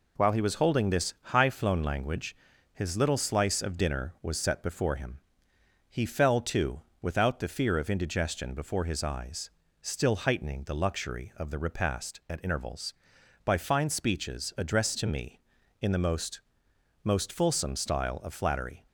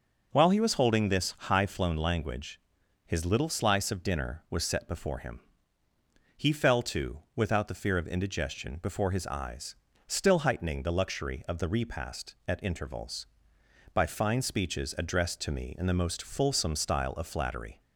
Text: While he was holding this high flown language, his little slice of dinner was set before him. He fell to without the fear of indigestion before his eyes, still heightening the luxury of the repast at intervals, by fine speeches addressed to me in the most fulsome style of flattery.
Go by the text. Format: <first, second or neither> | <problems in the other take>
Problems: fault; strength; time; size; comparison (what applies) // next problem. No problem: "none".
second | pauses between "to" and "without"; slight; at 6.8 s; 0.22 s long; slight in the second // says "most" twice; at 17.0 s